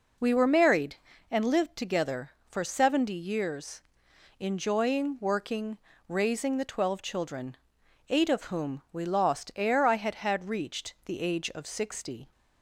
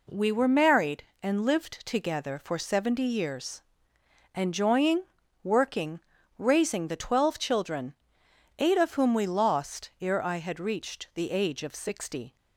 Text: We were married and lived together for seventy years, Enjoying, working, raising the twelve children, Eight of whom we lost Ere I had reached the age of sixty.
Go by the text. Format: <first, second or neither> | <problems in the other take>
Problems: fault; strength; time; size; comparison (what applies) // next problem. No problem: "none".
second | says "had" twice; at 10.1 s